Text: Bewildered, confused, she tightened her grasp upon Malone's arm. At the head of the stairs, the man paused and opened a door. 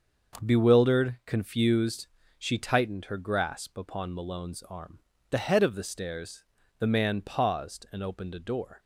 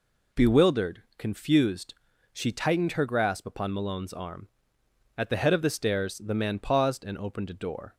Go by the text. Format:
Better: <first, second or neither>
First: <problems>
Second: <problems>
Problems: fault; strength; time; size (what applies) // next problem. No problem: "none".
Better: second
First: starts louder than the rest; until 1.5 s; 6 dB // skips "At"; at 5.1 s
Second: none